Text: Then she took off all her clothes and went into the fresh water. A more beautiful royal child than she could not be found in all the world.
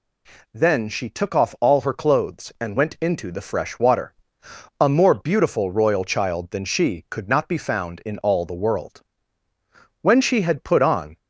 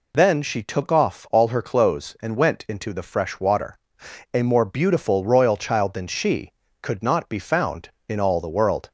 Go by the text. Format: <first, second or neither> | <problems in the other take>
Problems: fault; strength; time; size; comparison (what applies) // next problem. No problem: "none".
second | goes on to say "When she had put on"; noticeable; from 9.9 s on; 1.1 s long